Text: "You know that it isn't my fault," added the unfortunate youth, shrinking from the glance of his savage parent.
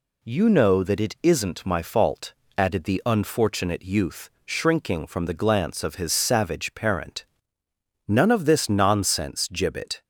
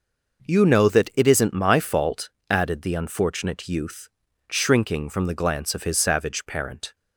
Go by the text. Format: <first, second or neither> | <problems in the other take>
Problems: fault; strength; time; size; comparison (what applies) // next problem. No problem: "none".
second | goes on to say "None of this nonsense Gibbet"; strong; from 8.0 s on; 1.9 s long